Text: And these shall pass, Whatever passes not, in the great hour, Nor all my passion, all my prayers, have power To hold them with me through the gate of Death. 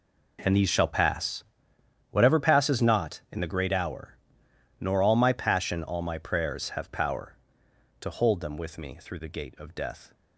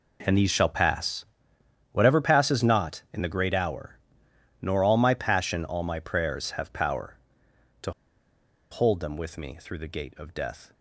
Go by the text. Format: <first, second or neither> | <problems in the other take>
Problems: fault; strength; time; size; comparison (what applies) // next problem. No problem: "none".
first | pauses between "To" and "hold"; noticeable; at 7.9 s; 0.80 s long